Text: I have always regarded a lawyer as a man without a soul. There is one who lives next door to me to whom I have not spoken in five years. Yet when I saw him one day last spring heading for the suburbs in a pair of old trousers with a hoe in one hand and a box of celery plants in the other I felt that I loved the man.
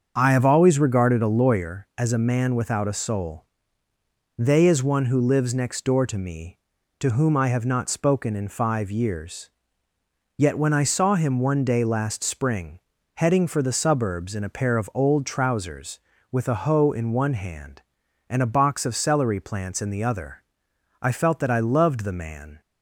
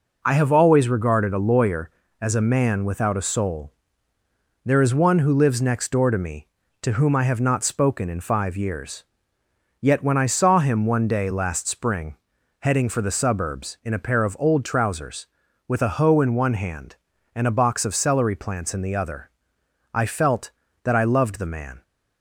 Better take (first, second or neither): second